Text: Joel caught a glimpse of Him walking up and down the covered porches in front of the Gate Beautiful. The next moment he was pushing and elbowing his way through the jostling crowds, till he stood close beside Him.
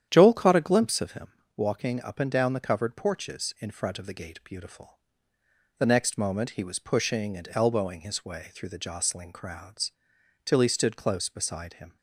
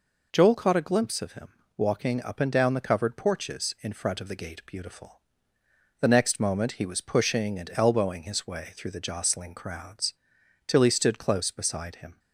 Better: second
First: starts louder than the rest; strong; until 1.4 s; 9.5 dB // pauses between "Him" and "walking"; slight; at 1.3 s; 0.26 s long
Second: pauses between "Him" and "walking"; slight; at 1.5 s; 0.26 s long

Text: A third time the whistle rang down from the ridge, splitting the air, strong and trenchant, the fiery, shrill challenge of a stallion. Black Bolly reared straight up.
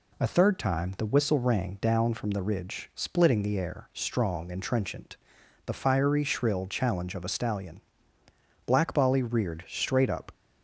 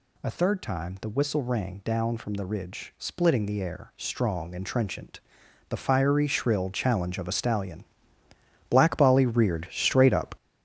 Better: first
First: none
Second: gets louder; strong; throughout; 8 dB

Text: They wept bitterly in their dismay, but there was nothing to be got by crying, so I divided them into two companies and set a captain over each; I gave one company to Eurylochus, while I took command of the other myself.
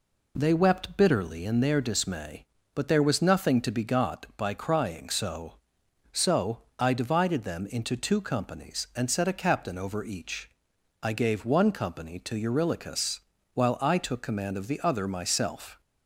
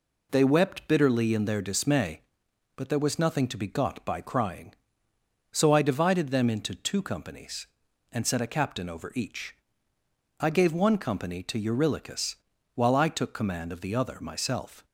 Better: second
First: says "so" twice; at 6.1 s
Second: none

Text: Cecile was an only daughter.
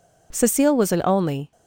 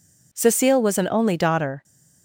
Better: second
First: stops before "daughter"; at 1.5 s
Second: none

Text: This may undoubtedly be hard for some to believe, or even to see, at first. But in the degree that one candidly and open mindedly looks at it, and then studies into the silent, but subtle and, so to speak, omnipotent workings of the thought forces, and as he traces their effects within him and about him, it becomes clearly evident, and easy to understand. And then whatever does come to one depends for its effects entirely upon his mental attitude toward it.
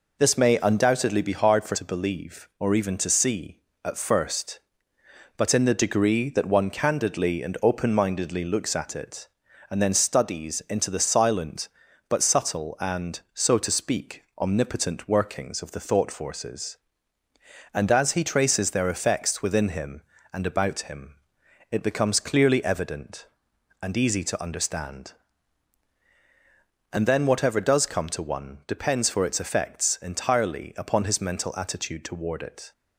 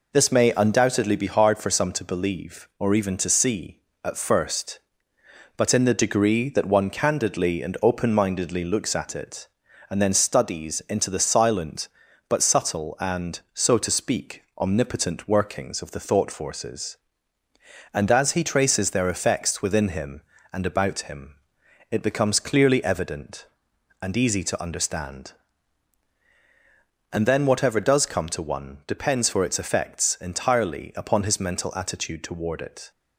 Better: second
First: skips "some"; at 1.7 s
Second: none

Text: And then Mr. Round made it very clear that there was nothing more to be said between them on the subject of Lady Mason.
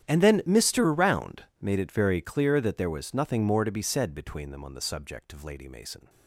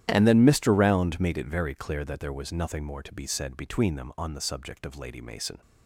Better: second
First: gets quieter; strong; throughout; 21.5 dB // starts louder than the rest; strong; until 1.1 s; 10.5 dB // pauses between "Round" and "made"; slight; at 1.4 s; 0.18 s long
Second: starts louder than the rest; strong; until 1.0 s; 11 dB

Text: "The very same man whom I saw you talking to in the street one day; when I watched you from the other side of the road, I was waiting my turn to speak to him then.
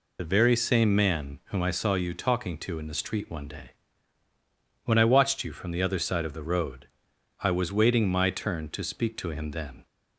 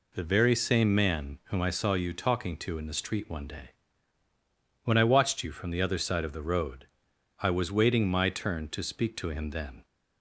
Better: second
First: loses the start of "The"; at 0.1 s; 45 ms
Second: none

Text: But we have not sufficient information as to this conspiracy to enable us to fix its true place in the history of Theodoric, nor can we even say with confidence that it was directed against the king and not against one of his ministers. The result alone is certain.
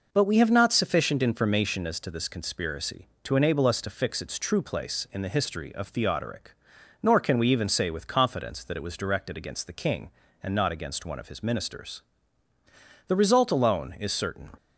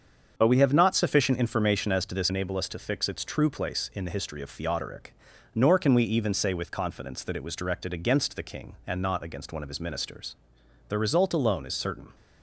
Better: first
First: none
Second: starts louder than the rest; strong; until 1.3 s; 7 dB // skips "conspiracy to"; at 2.2 s

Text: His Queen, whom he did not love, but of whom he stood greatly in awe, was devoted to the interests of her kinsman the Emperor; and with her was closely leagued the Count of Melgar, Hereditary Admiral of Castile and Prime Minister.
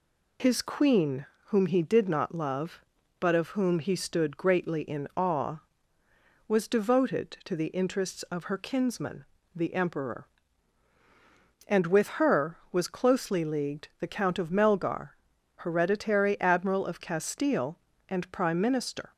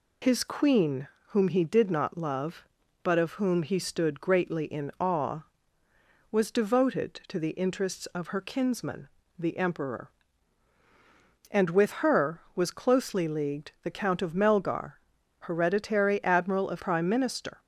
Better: first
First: pauses between "kinsman" and "the"; slight; at 9.2 s; 0.28 s long // pauses between "with" and "her"; slight; at 12.0 s; 0.16 s long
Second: pauses between "kinsman" and "the"; slight; at 9.0 s; 0.28 s long // pauses between "with" and "her"; slight; at 11.9 s; 0.16 s long // skips "Castile and"; at 16.8 s

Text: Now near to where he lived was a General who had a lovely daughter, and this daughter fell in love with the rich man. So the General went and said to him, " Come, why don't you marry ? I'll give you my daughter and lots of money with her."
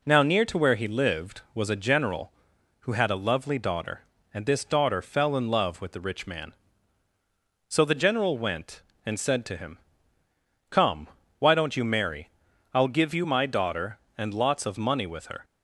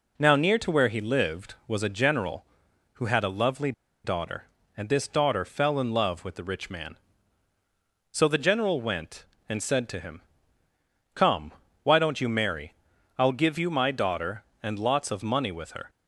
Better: first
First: none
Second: pauses between "lovely" and "daughter"; slight; at 3.7 s; 0.33 s long

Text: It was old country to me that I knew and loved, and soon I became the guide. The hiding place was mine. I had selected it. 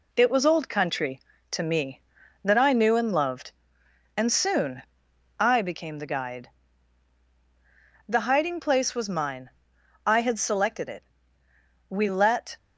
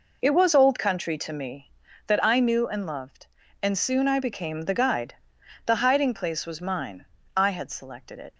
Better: second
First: pauses between "soon" and "I"; noticeable; at 4.8 s; 0.58 s long // goes on to say "We let"; noticeable; from 11.8 s on; 0.68 s long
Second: none

